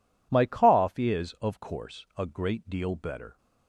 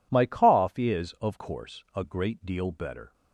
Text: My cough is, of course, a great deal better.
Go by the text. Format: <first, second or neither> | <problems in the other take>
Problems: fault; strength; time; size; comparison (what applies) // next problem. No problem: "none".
neither | none